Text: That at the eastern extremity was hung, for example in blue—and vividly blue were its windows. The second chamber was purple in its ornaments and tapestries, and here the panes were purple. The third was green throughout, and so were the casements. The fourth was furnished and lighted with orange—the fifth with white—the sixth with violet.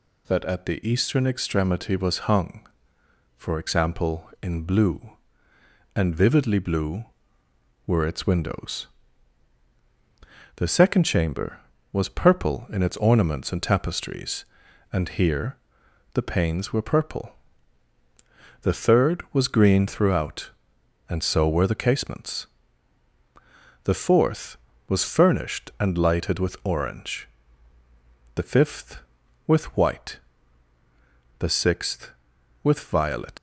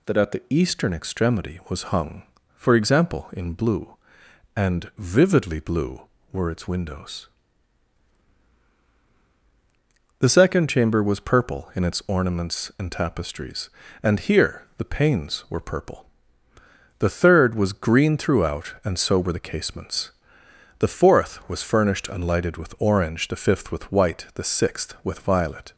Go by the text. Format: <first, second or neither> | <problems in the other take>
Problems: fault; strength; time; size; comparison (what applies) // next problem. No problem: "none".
second | pauses between "here" and "the"; noticeable; at 15.5 s; 0.58 s long // leaves "violet" unfinished; at 33.3 s; 70 ms